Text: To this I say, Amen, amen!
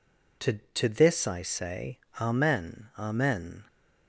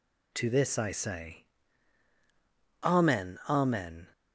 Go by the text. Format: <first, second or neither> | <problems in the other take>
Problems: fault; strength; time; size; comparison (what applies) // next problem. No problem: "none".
second | says "To" twice; at 0.7 s